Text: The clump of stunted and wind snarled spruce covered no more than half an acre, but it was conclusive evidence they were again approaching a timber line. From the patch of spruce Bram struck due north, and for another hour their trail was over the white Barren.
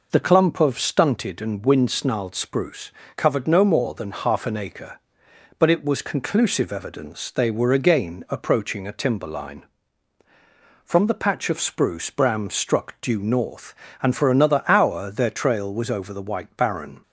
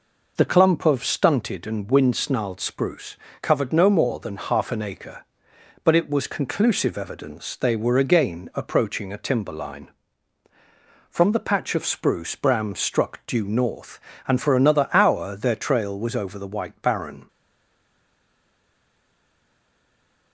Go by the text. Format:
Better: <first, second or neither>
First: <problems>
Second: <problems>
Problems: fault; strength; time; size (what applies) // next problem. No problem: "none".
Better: first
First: pauses between "spruce" and "covered"; slight; at 2.8 s; 0.26 s long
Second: pauses between "spruce" and "covered"; slight; at 3.1 s; 0.26 s long // stays silent after the last word; strong; from 17.2 s on; 3.1 s long